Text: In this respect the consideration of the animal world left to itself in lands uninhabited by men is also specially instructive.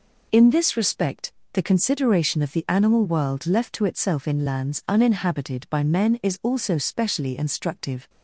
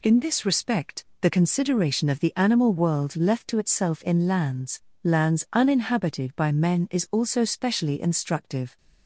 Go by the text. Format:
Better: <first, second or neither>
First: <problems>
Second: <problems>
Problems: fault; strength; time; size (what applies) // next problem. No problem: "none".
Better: first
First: pauses between "respect" and "the"; slight; at 1.3 s; 0.22 s long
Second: pauses between "respect" and "the"; slight; at 1.0 s; 0.16 s long // says "lands" twice; at 5.0 s